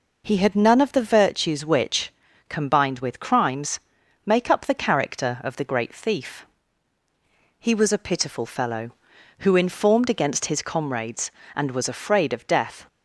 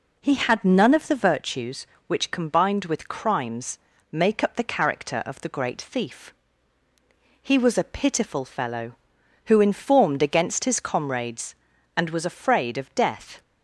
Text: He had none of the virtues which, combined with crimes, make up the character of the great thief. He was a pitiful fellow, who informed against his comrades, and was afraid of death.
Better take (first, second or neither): neither